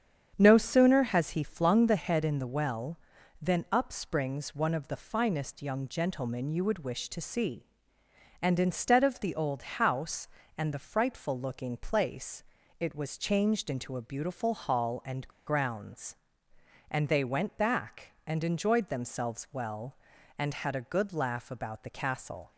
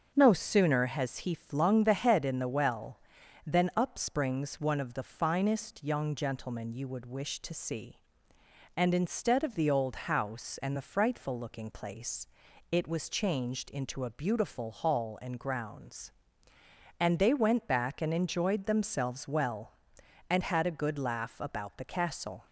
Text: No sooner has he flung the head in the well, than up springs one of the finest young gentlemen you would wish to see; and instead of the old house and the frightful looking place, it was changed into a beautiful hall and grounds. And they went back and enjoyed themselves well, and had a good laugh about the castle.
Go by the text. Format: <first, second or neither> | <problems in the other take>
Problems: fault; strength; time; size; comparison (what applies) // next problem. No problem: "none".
second | starts louder than the rest; strong; until 1.3 s; 8 dB; also in the second // pauses between "and" and "grounds"; slight; at 15.2 s; 0.21 s long